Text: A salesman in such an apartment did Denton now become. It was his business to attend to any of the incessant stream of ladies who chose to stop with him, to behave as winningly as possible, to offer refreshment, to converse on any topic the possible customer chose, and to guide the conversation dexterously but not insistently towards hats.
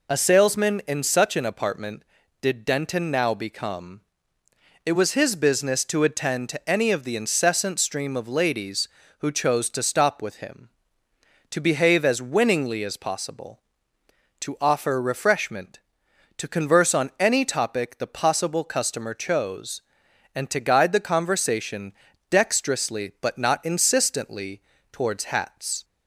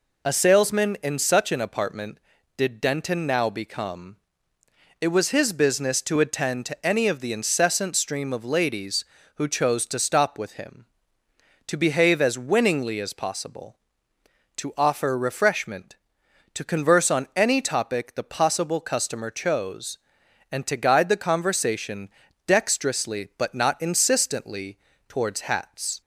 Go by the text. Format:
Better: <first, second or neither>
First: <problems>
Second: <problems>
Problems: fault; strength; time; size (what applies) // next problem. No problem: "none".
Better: neither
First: pauses between "conversation" and "dexterously"; slight; at 21.9 s; 0.36 s long // pauses between "insistently" and "towards"; slight; at 24.6 s; 0.28 s long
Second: pauses between "conversation" and "dexterously"; slight; at 22.0 s; 0.36 s long // pauses between "insistently" and "towards"; slight; at 24.7 s; 0.28 s long